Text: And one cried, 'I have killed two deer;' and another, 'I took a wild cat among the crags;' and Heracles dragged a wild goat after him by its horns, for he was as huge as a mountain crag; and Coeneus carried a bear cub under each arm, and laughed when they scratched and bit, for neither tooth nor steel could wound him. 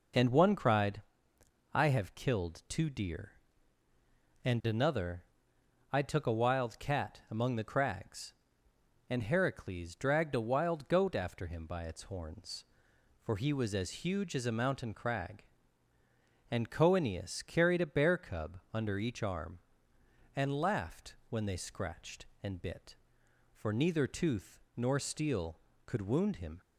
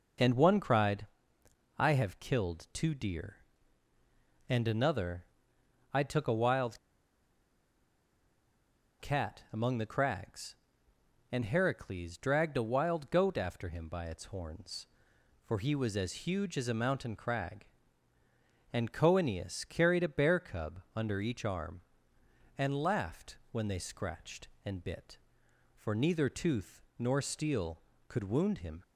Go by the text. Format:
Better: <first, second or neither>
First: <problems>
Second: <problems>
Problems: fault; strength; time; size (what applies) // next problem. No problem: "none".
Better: first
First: pauses between "cub" and "under"; slight; at 18.5 s; 0.16 s long // pauses between "laughed" and "when"; slight; at 21.1 s; 0.16 s long // pauses between "tooth" and "nor"; slight; at 24.5 s; 0.18 s long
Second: pauses between "wild" and "cat"; strong; at 6.7 s; 2.2 s long // pauses between "cub" and "under"; slight; at 20.8 s; 0.16 s long // pauses between "laughed" and "when"; slight; at 23.3 s; 0.16 s long // pauses between "tooth" and "nor"; slight; at 26.8 s; 0.18 s long